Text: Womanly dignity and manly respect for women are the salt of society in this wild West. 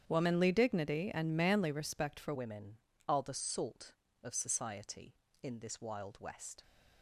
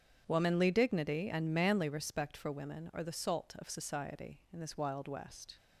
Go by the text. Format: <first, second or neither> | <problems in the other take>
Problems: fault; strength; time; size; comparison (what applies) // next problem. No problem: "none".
second | starts louder than the rest; strong; until 1.0 s; 8.5 dB; strong in the second // changes voice at "women"; from 2.3 s on; 4.3 s long